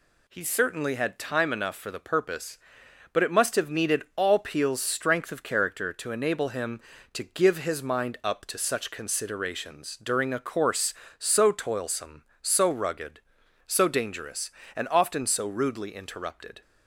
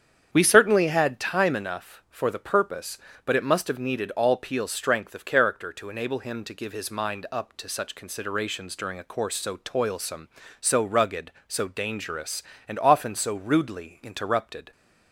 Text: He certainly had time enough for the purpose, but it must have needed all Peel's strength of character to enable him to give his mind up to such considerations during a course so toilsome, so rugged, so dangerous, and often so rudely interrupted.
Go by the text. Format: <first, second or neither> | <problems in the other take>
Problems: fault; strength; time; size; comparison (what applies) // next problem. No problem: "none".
first | starts louder than the rest; strong; until 1.3 s; 8 dB // says "We" for "He"; at 0.3 s